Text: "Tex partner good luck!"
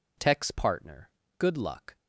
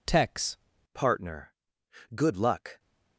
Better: first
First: pauses between "partner" and "good"; slight; at 1.0 s; 0.28 s long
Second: changes voice at "partner"; from 0.9 s on; 1.8 s long // pauses between "partner" and "good"; noticeable; at 1.5 s; 0.62 s long

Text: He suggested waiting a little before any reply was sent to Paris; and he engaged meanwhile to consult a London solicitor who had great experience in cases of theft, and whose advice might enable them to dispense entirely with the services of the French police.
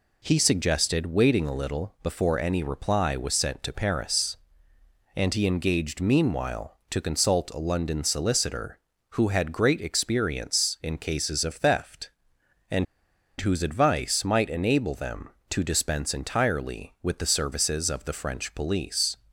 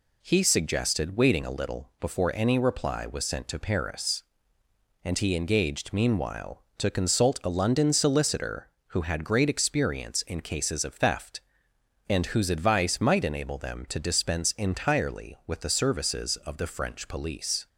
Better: second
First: pauses between "and" and "whose"; noticeable; at 12.8 s; 0.54 s long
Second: none

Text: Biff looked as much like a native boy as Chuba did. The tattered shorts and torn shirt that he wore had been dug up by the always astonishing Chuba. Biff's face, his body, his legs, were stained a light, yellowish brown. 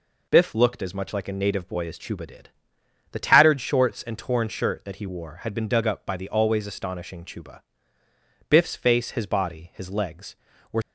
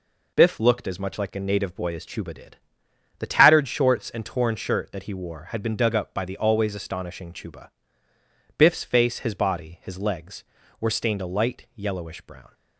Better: second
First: stops before "stained a light yellowish brown"; at 10.8 s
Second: none

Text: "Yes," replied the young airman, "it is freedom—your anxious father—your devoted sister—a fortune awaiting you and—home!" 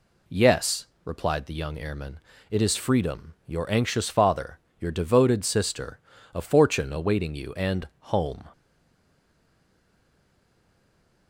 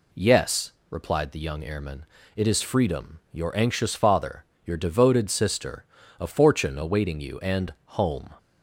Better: second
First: stays silent after the last word; strong; from 8.5 s on; 2.7 s long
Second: none

